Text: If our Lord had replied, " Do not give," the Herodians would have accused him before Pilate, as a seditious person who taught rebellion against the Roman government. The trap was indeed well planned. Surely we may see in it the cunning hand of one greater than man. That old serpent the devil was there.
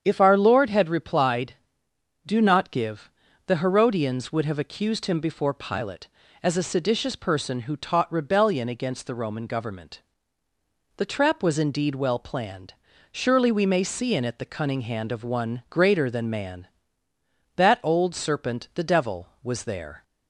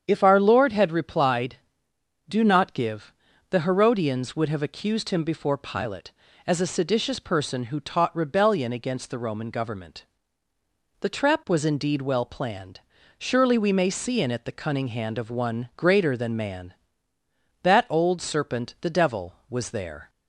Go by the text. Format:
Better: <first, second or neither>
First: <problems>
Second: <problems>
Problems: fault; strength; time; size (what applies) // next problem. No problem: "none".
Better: neither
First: starts louder than the rest; strong; until 1.0 s; 7 dB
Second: starts louder than the rest; strong; until 1.0 s; 7 dB